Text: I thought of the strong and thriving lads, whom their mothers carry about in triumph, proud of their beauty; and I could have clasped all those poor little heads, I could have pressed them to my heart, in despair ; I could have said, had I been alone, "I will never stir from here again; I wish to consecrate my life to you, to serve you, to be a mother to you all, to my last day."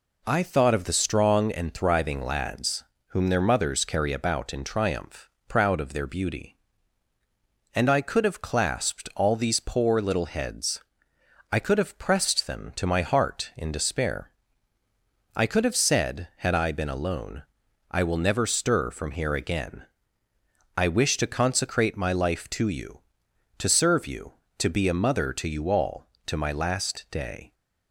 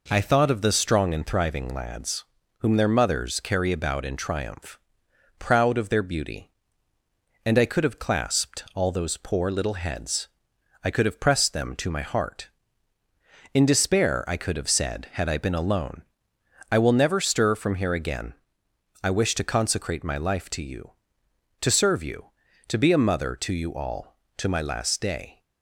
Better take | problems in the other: second | says "these" for "those"; at 9.3 s

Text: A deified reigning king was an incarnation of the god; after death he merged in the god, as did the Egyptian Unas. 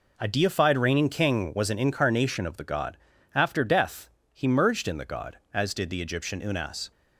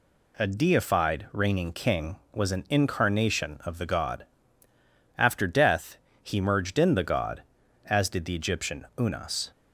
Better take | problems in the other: neither | pauses between "death" and "he"; slight; the same in both

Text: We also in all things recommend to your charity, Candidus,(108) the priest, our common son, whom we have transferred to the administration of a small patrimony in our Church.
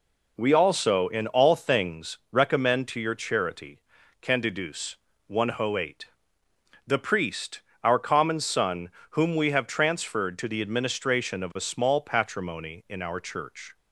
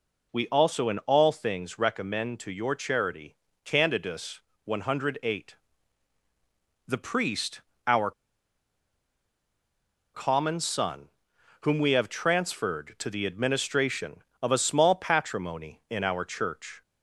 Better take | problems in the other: first | pauses between "our" and "common"; strong; at 8.1 s; 2.0 s long

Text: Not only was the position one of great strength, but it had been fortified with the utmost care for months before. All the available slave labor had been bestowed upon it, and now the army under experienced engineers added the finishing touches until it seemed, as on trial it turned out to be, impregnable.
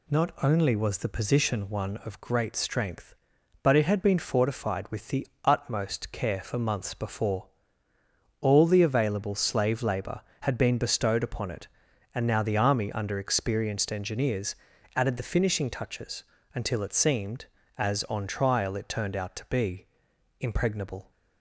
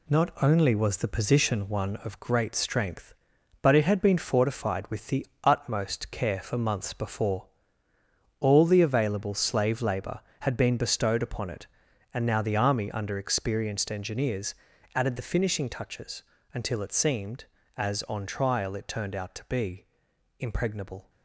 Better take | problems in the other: first | gets quieter; noticeable; throughout; 5.5 dB // pauses between "the" and "utmost"; slight; at 5.2 s; 0.18 s long; slight in the first // pauses between "engineers" and "added"; at 14.5 s; 0.40 s long; also in the first // pauses between "touches" and "until"; slight; at 16.2 s; 0.30 s long; slight in the first

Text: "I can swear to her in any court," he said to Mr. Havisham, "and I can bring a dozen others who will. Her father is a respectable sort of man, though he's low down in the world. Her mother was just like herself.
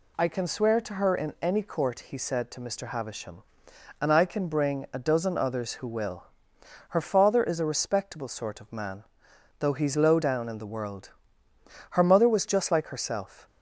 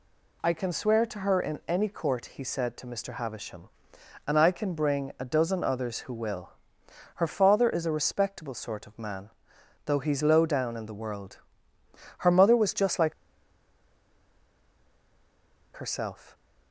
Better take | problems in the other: first | pauses between "like" and "herself"; strong; at 13.1 s; 2.6 s long

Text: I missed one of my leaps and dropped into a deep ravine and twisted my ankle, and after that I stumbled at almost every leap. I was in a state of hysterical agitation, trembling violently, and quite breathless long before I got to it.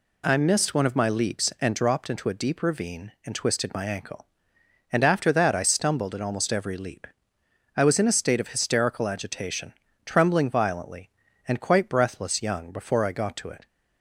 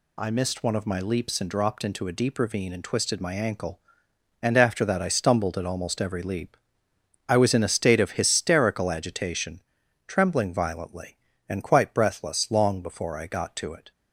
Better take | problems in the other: second | says "young" for "long"; at 12.4 s

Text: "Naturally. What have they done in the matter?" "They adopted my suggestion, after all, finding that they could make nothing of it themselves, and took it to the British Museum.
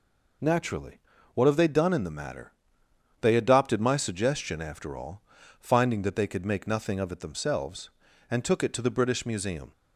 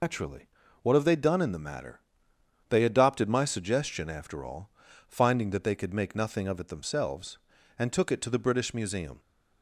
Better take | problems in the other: first | loses the start of "Naturally"; at 0.0 s; 125 ms

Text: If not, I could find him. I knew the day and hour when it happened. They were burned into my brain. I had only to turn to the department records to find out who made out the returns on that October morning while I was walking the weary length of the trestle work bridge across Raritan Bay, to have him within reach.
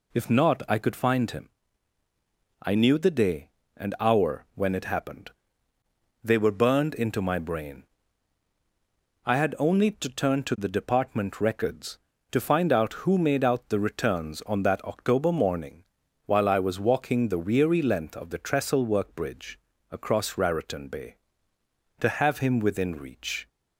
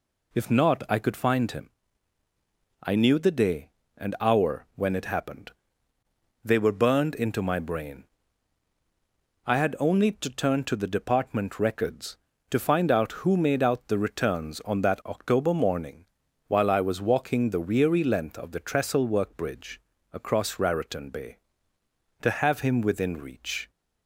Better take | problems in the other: neither | pauses between "morning" and "while"; the same in both // pauses between "bridge" and "across"; slight; the same in both

